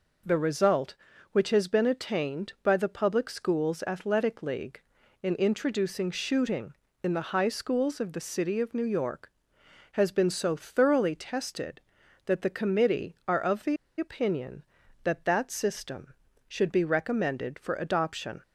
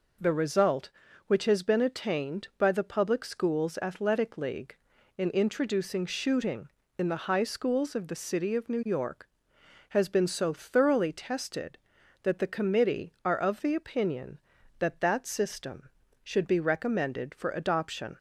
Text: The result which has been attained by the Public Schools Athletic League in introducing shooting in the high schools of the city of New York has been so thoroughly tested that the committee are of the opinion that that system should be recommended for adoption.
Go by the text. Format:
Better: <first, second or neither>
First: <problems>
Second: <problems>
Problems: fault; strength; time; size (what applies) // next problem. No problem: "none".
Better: second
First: pauses between "the" and "opinion"; slight; at 13.7 s; 0.22 s long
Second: none